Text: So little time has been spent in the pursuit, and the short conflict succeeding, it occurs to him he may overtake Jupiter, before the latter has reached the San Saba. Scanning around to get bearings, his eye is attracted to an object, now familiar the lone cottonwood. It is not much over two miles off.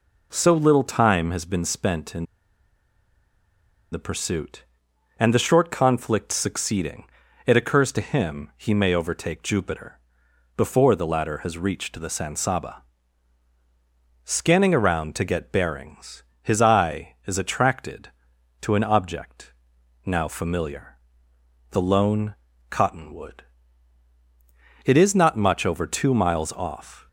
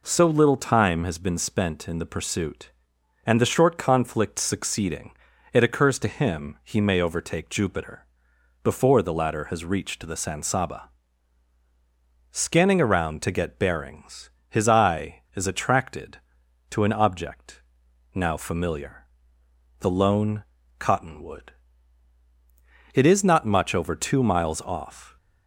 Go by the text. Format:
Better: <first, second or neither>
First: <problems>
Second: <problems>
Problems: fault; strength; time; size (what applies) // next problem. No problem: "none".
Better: second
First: pauses between "in" and "the"; strong; at 2.2 s; 1.6 s long // pauses between "familiar" and "the"; noticeable; at 20.9 s; 0.78 s long // pauses between "lone" and "cottonwood"; slight; at 22.3 s; 0.34 s long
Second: pauses between "familiar" and "the"; noticeable; at 19.0 s; 0.78 s long // pauses between "lone" and "cottonwood"; slight; at 20.4 s; 0.34 s long